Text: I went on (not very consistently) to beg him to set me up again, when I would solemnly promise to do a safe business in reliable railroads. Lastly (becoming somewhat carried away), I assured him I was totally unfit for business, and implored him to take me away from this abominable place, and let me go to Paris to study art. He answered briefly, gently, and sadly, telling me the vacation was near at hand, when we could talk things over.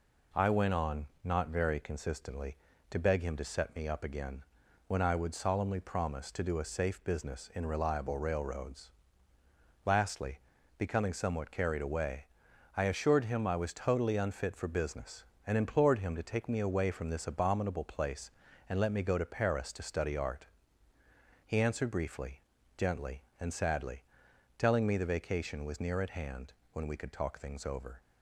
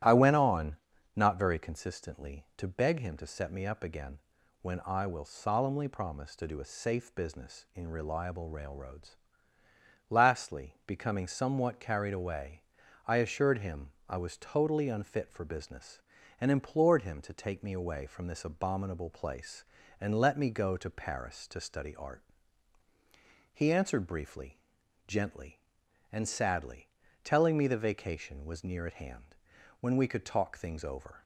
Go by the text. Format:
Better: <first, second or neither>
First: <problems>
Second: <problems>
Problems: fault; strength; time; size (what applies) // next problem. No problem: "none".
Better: first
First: none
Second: starts louder than the rest; strong; until 1.4 s; 12.5 dB // says "will" for "would"; at 5.0 s // pauses between "him" and "I"; slight; at 13.9 s; 0.18 s long